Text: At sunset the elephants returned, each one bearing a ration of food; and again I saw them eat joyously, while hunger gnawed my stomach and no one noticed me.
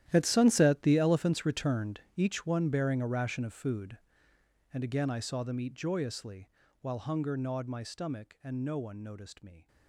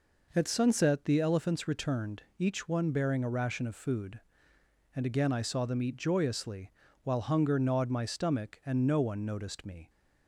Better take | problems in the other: second | gets quieter; strong; throughout; 17 dB

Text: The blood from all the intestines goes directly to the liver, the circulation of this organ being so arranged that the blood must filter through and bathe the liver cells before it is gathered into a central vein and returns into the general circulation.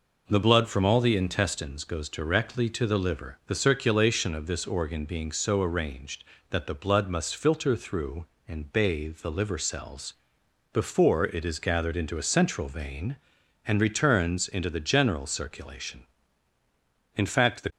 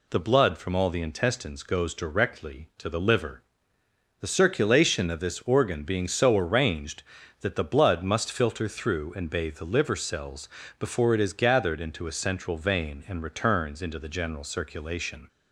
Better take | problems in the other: second | pauses between "cells" and "before"; noticeable; at 10.1 s; 0.60 s long; slight in the second // goes on to say "In fact the"; from 17.1 s on; 0.54 s long

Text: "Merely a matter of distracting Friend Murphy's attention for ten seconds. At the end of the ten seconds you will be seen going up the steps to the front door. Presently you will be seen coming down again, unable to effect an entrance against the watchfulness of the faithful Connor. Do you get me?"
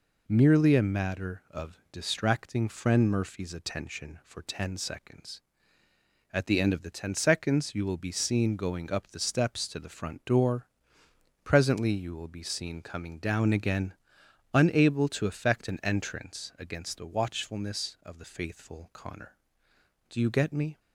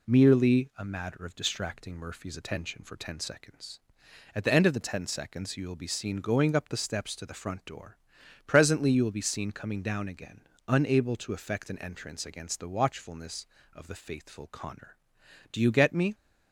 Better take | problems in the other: first | skips "Friend"; at 1.9 s

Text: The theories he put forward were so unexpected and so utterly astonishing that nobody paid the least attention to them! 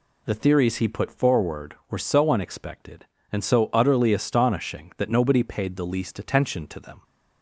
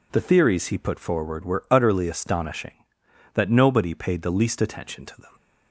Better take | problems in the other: first | skips "so unexpected and so"; at 1.6 s

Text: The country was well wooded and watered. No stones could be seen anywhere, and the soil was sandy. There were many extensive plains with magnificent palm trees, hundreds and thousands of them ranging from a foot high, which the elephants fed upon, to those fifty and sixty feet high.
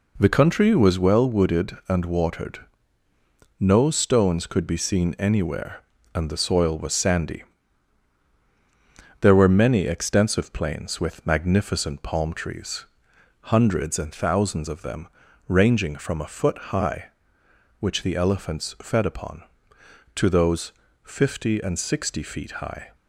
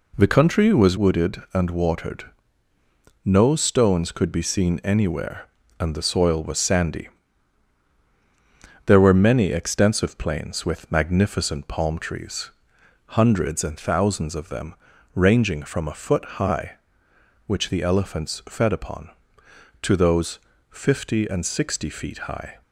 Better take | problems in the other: first | skips "well"; at 0.9 s // pauses between "them" and "ranging"; at 14.7 s; 0.40 s long; also in the first // pauses between "those" and "fifty"; slight; at 20.3 s; 0.32 s long; slight in the first

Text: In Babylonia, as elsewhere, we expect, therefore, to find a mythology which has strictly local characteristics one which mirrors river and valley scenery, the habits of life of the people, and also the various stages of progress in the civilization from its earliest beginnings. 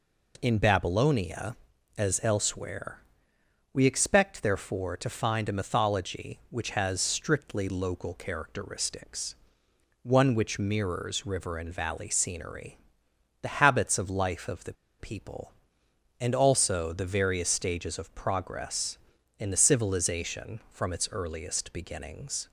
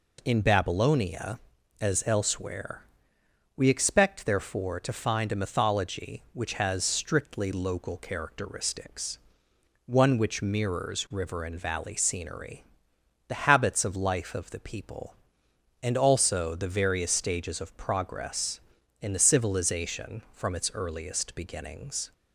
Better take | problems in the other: second | pauses between "characteristics" and "one"; noticeable; at 9.3 s; 0.68 s long; noticeable in the second // pauses between "the" and "people"; slight; at 14.7 s; 0.25 s long

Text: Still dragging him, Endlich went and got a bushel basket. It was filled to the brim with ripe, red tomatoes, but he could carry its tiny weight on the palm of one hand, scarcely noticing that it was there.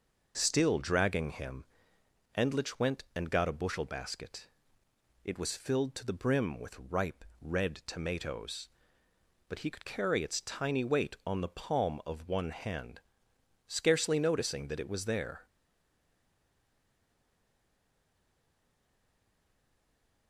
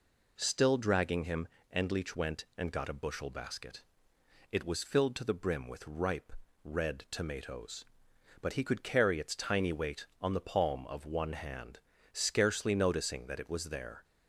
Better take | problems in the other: second | stays silent after the last word; strong; from 15.4 s on; 4.8 s long

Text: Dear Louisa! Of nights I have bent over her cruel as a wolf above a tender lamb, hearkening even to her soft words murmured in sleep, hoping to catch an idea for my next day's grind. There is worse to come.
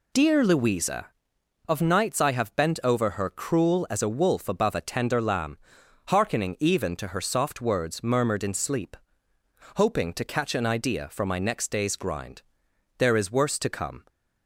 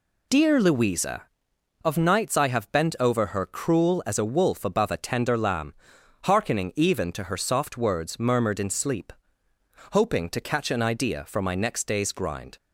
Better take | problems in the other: first | stops before "There is worse to come"; at 12.5 s

